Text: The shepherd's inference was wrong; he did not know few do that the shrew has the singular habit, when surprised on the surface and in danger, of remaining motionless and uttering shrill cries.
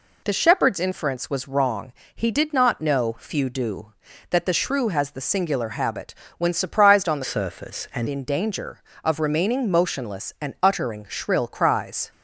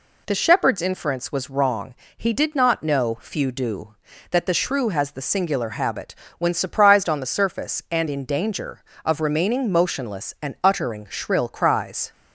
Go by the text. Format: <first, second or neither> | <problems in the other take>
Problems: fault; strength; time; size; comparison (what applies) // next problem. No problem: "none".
second | changes voice from "surface" to "and"; from 7.2 to 8.0 s; 0.8 s long